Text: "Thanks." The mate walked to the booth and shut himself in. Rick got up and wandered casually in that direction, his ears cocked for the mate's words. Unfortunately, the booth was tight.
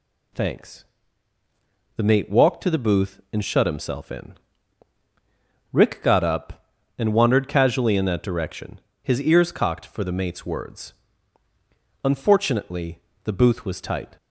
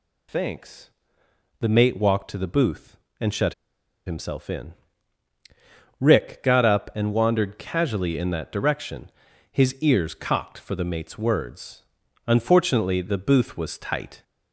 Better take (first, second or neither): first